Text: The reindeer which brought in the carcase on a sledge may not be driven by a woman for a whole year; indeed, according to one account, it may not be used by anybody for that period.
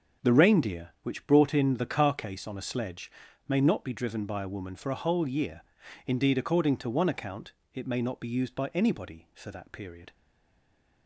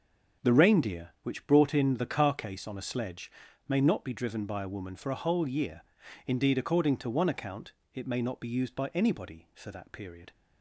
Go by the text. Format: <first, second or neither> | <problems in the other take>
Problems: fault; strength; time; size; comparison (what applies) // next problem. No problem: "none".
second | starts louder than the rest; until 1.3 s; 7 dB; also in the second // pauses between "sledge" and "may"; at 3.0 s; 0.38 s long; also in the second // stays silent after the last word; slight; from 10.1 s on; 0.9 s long